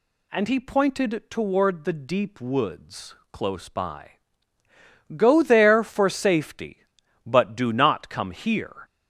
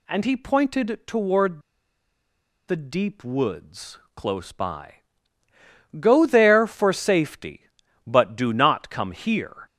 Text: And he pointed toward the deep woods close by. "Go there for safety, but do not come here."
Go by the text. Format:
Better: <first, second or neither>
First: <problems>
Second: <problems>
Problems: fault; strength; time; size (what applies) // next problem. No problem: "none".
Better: first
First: pauses between "woods" and "close"; slight; at 3.1 s; 0.18 s long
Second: pauses between "toward" and "the"; at 1.6 s; 1.0 s long // pauses between "woods" and "close"; slight; at 3.9 s; 0.18 s long